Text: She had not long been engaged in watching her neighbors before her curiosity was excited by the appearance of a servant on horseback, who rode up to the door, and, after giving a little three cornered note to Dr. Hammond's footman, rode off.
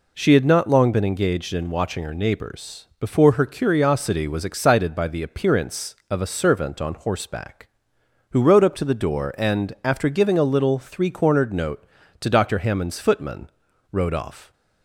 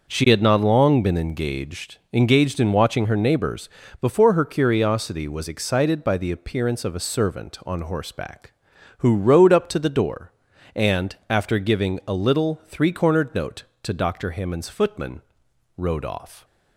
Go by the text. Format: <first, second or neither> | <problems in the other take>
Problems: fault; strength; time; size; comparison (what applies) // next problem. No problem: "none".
first | says "engaged" twice; at 2.1 s // pauses between "neighbors" and "before"; slight; at 3.6 s; 0.32 s long